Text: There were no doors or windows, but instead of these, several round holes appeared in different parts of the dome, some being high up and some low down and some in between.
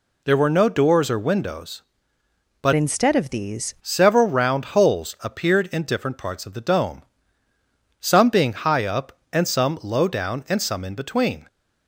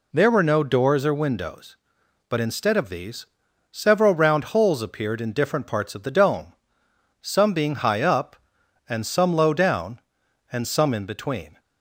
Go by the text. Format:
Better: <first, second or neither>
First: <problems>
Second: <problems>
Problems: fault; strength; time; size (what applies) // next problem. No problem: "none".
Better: second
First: changes voice from "instead" to "these"; from 2.7 to 3.7 s; 1.0 s long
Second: none